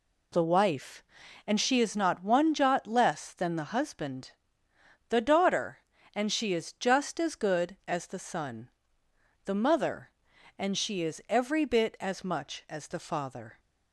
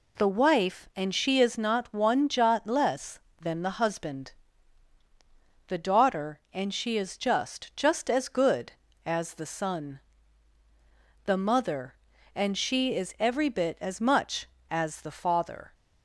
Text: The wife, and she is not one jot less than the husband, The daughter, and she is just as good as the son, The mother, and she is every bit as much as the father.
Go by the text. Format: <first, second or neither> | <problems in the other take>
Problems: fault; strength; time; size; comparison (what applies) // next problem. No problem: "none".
first | says "just" twice; at 7.7 s